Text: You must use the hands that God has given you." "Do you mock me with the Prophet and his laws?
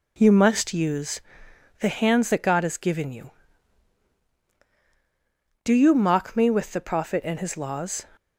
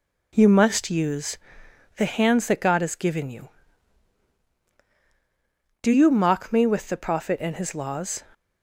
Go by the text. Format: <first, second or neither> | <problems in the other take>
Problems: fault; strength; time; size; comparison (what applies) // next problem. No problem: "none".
neither | pauses between "use" and "the"; noticeable; the same in both